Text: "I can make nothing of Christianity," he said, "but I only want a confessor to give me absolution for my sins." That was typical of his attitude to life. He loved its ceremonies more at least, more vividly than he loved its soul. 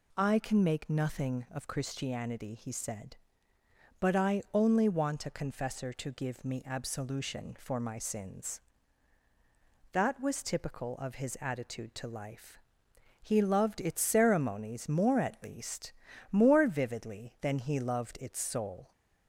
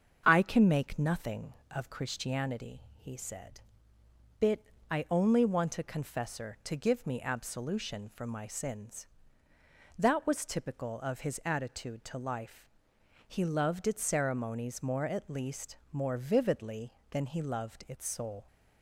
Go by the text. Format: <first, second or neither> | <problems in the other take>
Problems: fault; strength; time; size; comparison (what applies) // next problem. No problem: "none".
first | starts louder than the rest; until 1.2 s; 6.5 dB // says "bit" for "but"; at 4.4 s